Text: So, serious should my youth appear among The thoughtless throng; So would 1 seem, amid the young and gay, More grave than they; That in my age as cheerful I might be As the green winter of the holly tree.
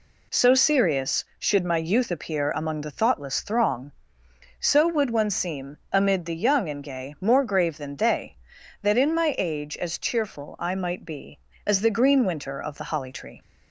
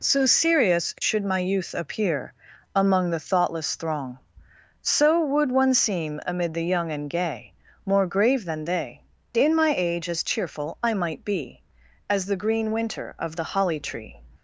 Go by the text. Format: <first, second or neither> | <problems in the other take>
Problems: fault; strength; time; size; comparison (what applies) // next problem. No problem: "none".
first | pauses between "appear" and "among"; at 2.3 s; 0.42 s long // skips "That"; at 9.2 s